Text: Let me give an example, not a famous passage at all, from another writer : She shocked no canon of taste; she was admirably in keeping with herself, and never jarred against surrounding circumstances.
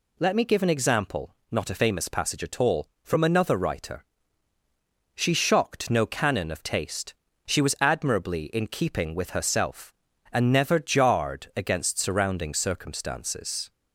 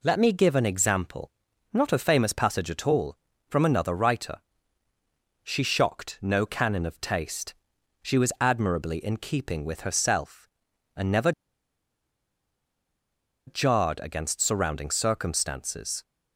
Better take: first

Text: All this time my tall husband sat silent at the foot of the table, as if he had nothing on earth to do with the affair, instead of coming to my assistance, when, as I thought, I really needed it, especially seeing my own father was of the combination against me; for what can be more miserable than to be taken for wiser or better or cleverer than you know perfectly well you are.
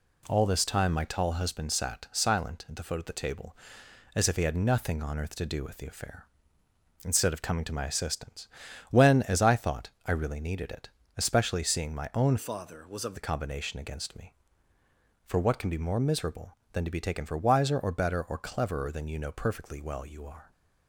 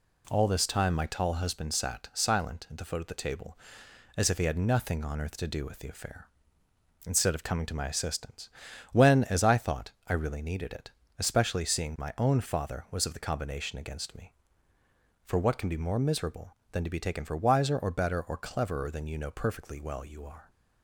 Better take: second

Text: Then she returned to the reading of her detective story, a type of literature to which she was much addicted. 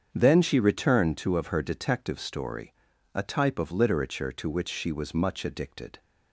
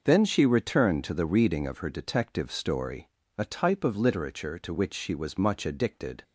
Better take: second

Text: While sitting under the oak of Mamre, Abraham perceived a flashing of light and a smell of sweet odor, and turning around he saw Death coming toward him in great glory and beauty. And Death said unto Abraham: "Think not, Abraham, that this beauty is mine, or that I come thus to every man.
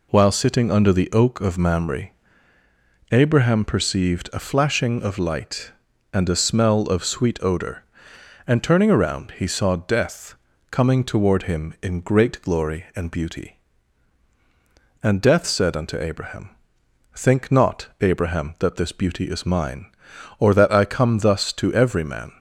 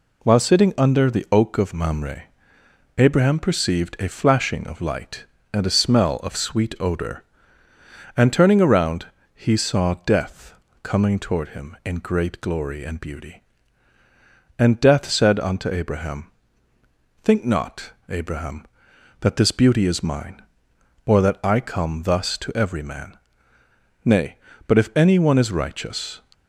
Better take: first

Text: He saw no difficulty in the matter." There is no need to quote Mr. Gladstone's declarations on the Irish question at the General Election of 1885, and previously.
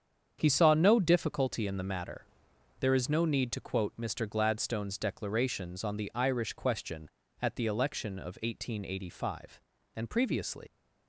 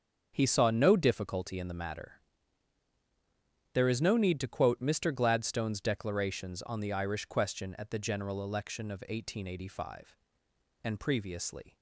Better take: second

